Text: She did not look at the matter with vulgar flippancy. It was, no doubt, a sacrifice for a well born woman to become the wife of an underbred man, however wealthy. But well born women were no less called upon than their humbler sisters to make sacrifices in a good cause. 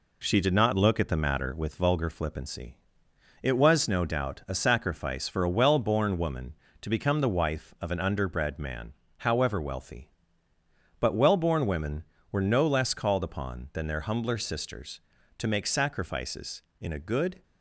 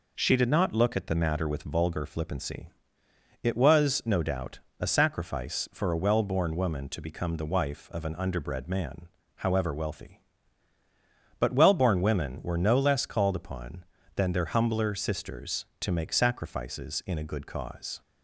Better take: second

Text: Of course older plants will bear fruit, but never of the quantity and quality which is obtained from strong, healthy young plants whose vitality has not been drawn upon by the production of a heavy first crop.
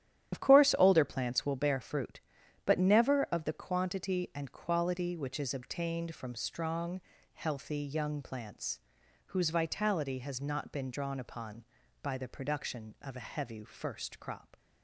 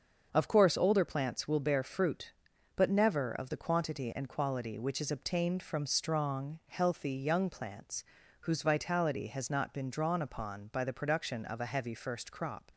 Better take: second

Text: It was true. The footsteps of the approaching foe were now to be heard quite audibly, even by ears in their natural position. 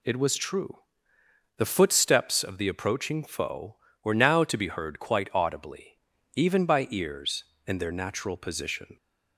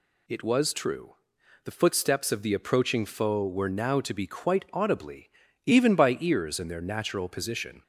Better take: first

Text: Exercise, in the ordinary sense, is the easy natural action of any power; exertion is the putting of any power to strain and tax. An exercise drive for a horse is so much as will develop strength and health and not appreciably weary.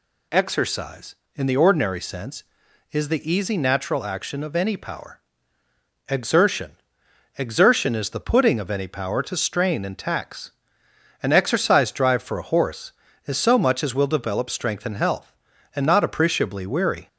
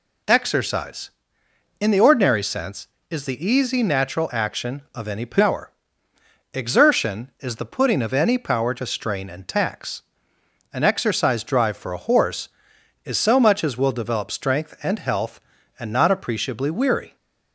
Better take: second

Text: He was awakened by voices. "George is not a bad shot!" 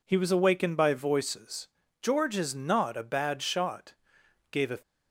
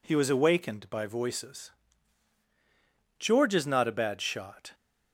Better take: second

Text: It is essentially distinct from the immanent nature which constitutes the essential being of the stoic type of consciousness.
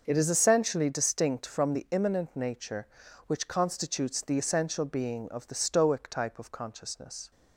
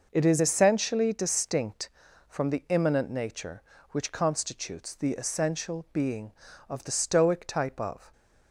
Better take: first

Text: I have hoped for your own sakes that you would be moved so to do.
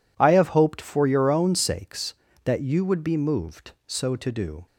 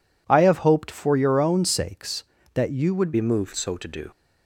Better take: first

